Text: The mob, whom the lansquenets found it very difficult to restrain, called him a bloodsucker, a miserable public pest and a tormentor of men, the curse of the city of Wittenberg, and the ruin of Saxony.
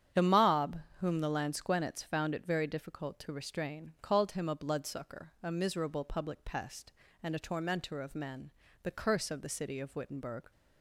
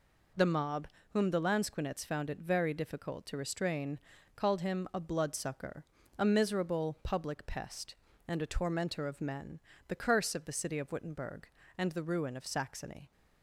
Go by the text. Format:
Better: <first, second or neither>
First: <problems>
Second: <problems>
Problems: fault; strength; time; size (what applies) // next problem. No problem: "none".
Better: second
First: starts louder than the rest; strong; until 1.3 s; 8.5 dB // stops before "and the ruin of Saxony"; at 10.5 s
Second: none